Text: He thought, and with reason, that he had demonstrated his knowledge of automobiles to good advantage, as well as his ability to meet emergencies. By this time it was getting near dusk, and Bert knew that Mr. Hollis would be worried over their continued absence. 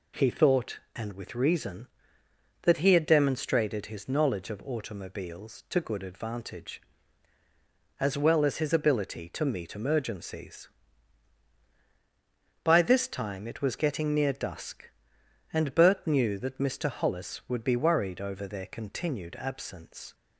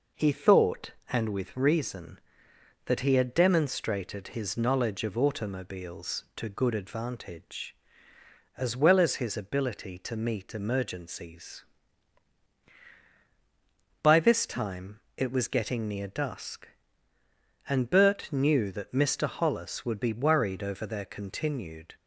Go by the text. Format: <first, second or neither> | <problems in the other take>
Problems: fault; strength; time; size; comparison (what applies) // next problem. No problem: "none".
first | pauses between "time" and "it"; slight; at 15.0 s; 0.16 s long // stops before "absence"; at 21.9 s